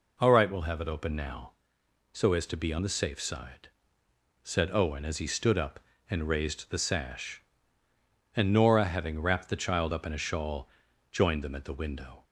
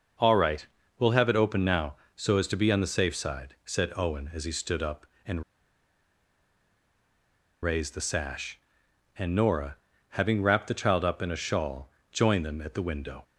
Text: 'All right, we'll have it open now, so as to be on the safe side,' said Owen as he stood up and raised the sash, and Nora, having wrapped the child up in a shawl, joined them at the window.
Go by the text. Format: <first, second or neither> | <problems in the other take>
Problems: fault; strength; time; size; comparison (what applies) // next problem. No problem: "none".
first | pauses between "and" and "raised"; strong; at 5.4 s; 2.2 s long